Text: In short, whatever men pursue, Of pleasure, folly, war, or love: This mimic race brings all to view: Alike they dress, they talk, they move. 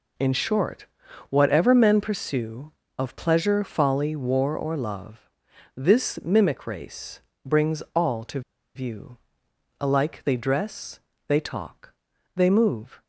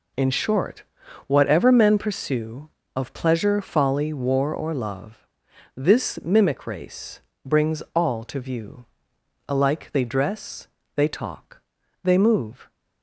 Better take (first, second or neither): second